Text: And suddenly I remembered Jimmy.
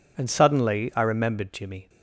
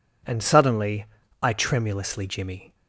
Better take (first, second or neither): first